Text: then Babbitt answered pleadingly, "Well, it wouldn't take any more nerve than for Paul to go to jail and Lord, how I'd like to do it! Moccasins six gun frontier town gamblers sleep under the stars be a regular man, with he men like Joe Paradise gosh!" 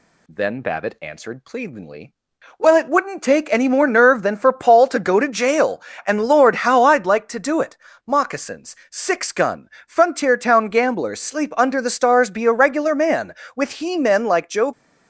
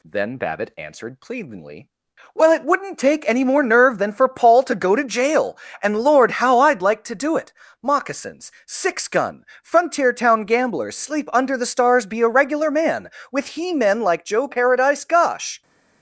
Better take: second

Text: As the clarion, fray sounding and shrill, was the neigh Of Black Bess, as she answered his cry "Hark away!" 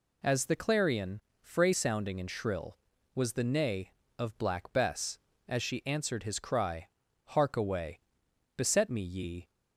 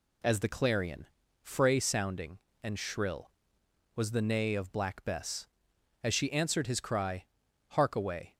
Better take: second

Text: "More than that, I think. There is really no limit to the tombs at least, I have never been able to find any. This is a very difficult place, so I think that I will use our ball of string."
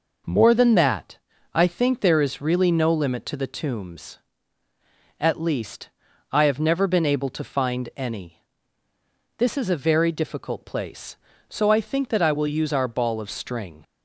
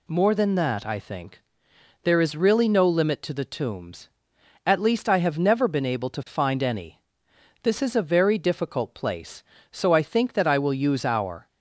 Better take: first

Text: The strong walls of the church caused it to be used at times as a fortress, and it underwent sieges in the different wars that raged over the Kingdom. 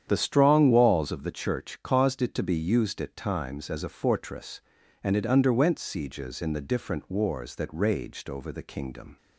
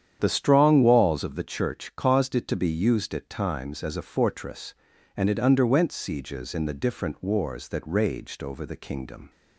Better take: neither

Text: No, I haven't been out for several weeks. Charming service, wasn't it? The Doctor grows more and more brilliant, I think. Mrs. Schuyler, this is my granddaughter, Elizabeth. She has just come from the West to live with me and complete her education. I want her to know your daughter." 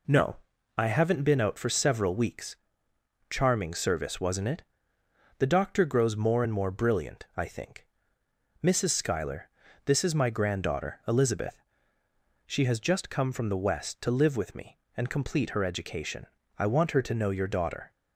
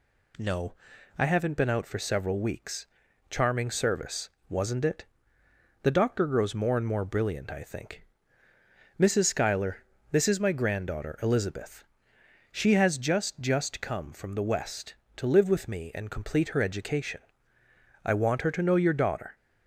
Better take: first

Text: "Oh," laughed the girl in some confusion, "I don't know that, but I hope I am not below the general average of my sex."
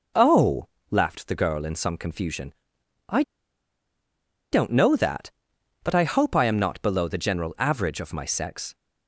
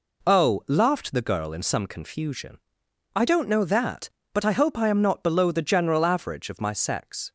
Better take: second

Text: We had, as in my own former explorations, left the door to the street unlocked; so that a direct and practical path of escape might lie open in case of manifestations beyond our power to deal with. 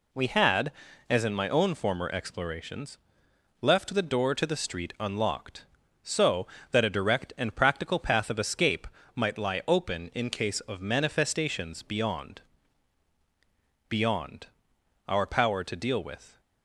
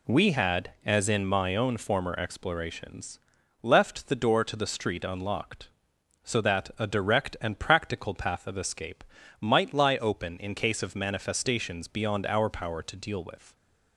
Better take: second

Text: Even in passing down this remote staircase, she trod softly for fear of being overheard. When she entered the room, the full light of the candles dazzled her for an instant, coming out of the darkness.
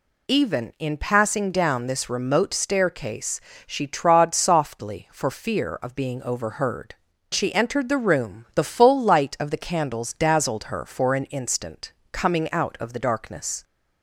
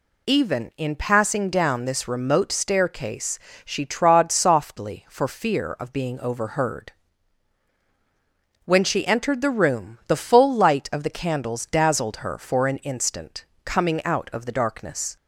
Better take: second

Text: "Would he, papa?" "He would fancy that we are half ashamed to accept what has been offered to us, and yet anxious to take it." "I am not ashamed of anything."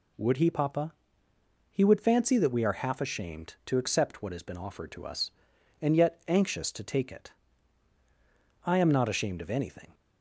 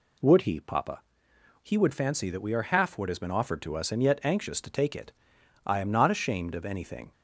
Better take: first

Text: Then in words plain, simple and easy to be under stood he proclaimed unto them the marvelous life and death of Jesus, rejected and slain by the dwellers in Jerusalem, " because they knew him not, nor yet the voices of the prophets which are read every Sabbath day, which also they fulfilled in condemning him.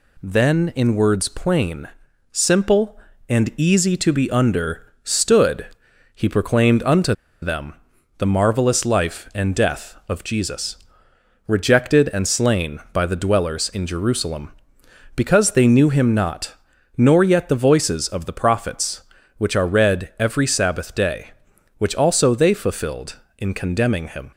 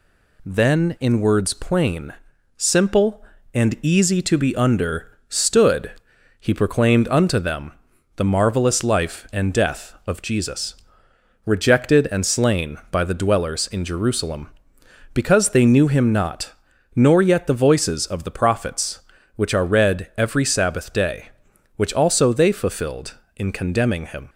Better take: second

